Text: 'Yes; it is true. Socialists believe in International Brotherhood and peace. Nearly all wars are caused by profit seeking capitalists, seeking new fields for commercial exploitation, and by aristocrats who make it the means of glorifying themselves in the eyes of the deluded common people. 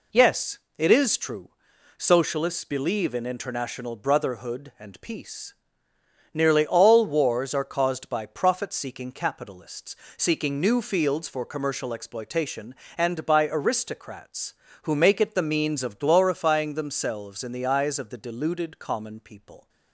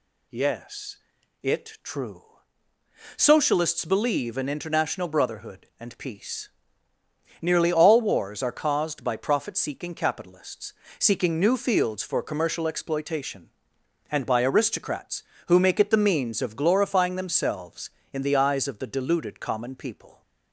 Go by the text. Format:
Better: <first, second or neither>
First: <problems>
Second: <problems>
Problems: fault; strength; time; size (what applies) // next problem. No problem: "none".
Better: first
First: none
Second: skips "is"; at 1.8 s